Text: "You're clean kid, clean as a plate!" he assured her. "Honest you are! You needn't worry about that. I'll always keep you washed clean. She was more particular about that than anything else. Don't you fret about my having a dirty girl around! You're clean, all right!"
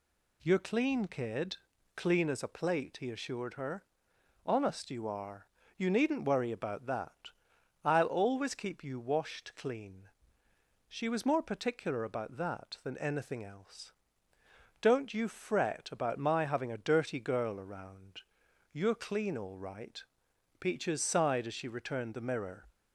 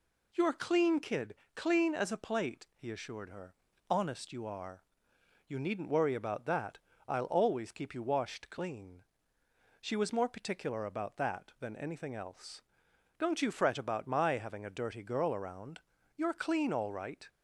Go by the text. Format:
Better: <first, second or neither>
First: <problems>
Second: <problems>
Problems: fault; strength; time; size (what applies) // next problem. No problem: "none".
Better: second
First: goes on to say "Peaches sighed as she returned the mirror"; strong; from 20.5 s on; 2.0 s long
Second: none